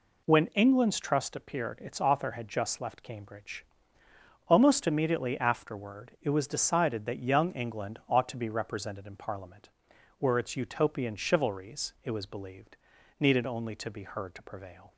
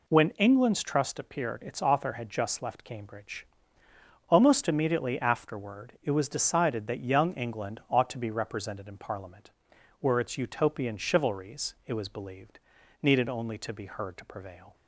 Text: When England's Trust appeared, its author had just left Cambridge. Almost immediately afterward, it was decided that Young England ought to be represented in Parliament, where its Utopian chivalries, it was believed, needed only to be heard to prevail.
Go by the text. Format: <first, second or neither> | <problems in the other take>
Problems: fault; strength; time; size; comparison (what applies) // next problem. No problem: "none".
neither | none